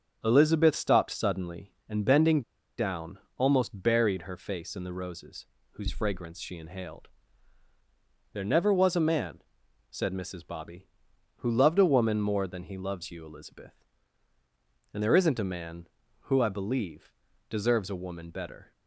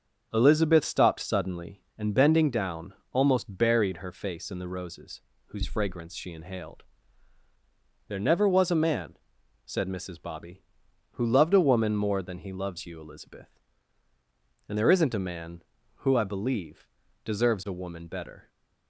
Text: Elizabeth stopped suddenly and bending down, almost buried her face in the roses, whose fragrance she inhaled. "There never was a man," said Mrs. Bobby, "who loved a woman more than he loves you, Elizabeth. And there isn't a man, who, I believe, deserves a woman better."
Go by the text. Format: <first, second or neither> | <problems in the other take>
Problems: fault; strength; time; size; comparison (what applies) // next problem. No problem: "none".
second | starts louder than the rest; strong; until 1.2 s; 7.5 dB; strong in the second // pauses between "bending" and "down"; at 2.4 s; 0.36 s long